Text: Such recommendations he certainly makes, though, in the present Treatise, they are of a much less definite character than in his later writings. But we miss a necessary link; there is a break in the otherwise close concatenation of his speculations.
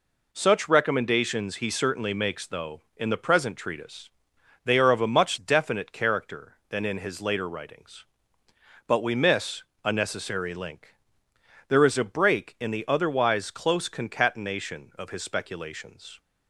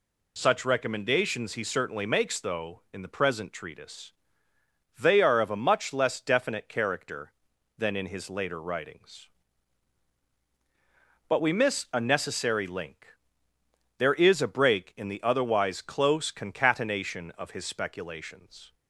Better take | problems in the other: second | skips "less"; at 5.3 s // pauses between "miss" and "a"; slight; at 9.6 s; 0.22 s long

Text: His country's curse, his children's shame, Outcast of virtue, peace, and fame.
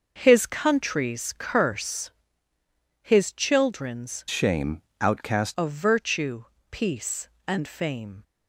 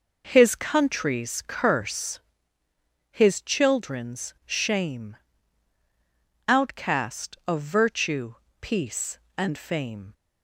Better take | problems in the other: second | changes voice from "shame" to "Outcast"; from 4.2 to 5.5 s; 1.3 s long

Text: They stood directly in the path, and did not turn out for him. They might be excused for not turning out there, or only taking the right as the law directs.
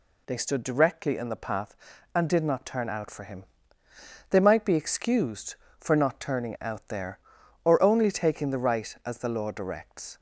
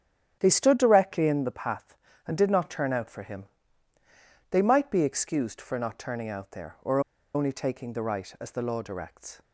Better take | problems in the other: first | starts louder than the rest; strong; until 1.4 s; 10 dB // pauses between "or" and "only"; slight; at 7.0 s; 0.34 s long

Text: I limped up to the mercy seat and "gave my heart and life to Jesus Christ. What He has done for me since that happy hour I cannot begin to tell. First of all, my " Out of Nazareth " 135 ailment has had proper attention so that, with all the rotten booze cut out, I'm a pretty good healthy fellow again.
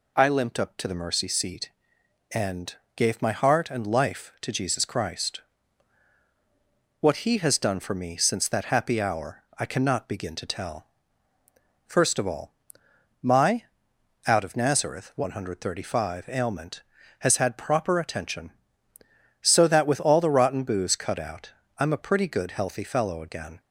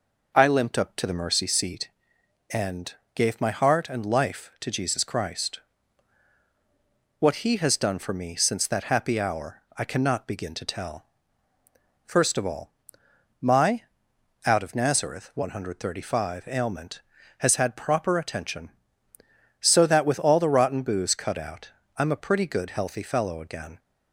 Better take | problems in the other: first | starts louder than the rest; noticeable; until 2.0 s; 5.5 dB // pauses between "and" and "gave"; slight; at 2.9 s; 0.22 s long; slight in the first

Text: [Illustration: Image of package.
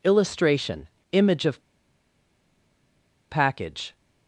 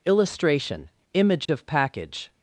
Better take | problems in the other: second | pauses between "of" and "package"; strong; at 1.5 s; 1.6 s long

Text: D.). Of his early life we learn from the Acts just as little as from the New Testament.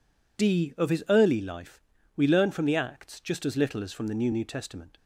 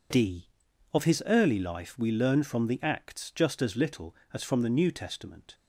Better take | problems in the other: second | pauses between "life" and "we"; slight; at 1.8 s; 0.34 s long // says "New" twice; at 4.3 s

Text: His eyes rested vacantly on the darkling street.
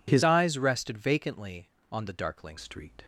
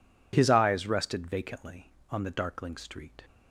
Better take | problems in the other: second | changes voice from "eyes" to "darkling"; from 0.2 to 2.5 s; 2.3 s long

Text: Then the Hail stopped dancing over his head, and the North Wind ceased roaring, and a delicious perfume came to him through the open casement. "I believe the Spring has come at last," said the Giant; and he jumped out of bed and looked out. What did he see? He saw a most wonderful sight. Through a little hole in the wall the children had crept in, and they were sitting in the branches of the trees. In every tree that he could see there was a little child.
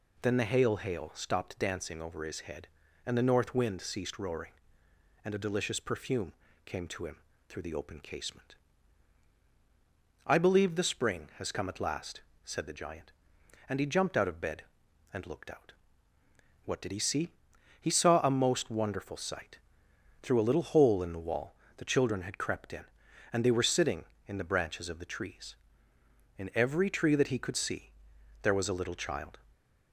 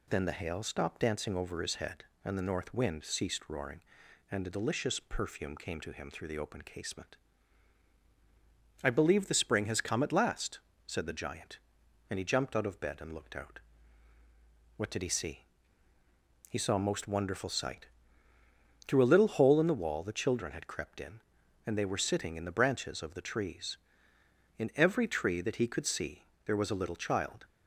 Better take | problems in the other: second | says "Hail" twice; at 0.7 s // pauses between "perfume" and "came"; slight; at 6.3 s; 0.34 s long // pauses between "him" and "through"; slight; at 7.1 s; 0.30 s long // pauses between "wall" and "the"; slight; at 21.5 s; 0.22 s long // pauses between "see" and "there"; noticeable; at 27.9 s; 0.50 s long; slight in the second

